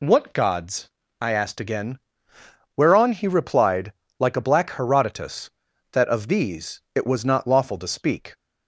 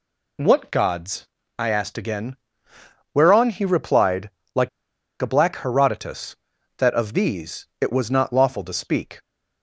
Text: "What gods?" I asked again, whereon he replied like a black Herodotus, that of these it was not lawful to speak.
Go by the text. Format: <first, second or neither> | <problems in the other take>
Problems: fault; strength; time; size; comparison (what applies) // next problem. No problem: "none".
first | pauses between "replied" and "like"; slight; at 4.2 s; 0.24 s long; slight in the first // pauses between "like" and "a"; noticeable; at 4.6 s; 0.52 s long